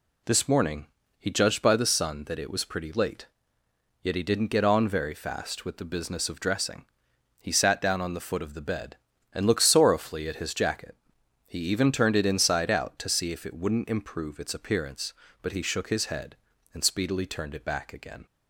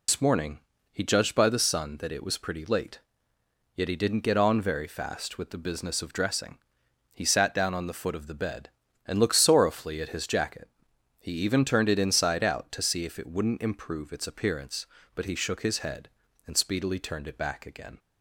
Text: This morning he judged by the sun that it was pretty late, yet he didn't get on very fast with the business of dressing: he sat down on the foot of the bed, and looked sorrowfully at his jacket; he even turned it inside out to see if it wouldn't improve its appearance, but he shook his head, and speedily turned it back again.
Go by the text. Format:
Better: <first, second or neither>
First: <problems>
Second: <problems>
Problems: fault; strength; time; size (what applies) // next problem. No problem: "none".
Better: first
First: pauses between "morning" and "he"; slight; at 0.8 s; 0.32 s long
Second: loses the start of "This"; at 0.0 s; 100 ms // pauses between "morning" and "he"; slight; at 0.5 s; 0.32 s long